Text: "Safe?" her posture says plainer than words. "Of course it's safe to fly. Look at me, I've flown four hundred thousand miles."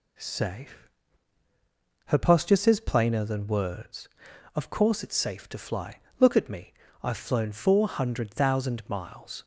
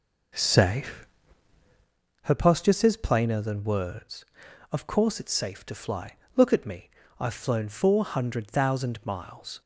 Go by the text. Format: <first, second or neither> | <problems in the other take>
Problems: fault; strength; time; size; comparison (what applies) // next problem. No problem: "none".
first | starts louder than the rest; noticeable; until 2.0 s; 5 dB